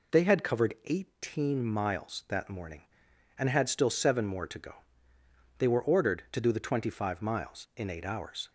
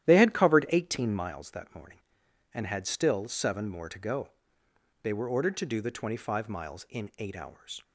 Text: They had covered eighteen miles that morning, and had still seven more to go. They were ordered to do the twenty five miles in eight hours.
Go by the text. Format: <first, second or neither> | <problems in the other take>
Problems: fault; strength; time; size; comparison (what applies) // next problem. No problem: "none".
first | starts louder than the rest; strong; until 1.4 s; 12 dB